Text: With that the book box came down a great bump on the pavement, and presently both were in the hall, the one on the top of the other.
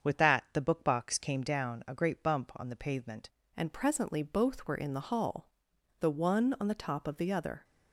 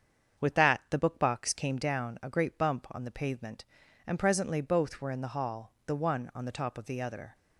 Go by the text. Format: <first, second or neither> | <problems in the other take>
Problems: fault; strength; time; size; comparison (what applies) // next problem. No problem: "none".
second | starts louder than the rest; until 1.1 s; 7 dB; strong in the second // changes voice at "and"; from 3.5 s on; 4.1 s long